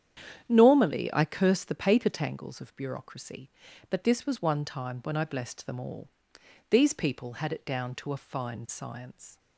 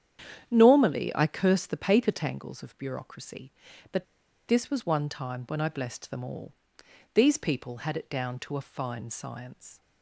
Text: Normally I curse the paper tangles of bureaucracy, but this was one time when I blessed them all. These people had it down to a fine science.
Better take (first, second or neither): first